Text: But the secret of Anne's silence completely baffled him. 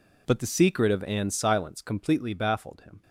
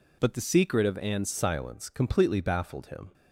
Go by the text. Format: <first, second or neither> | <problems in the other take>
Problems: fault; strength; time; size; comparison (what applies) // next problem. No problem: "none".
first | changes voice at "silence"; from 1.3 s on; 1.8 s long